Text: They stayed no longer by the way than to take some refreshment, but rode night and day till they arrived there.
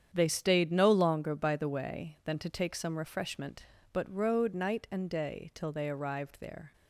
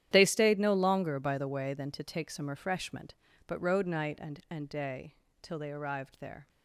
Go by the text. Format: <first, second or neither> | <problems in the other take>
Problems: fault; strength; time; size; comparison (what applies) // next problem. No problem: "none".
first | starts louder than the rest; strong; until 1.1 s; 11 dB; strong in the first // says "and" twice; at 4.4 s // pauses between "day" and "till"; slight; at 5.1 s; 0.24 s long